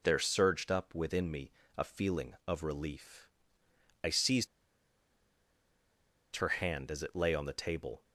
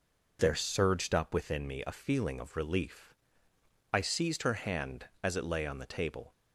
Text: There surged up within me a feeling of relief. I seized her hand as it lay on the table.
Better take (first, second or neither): second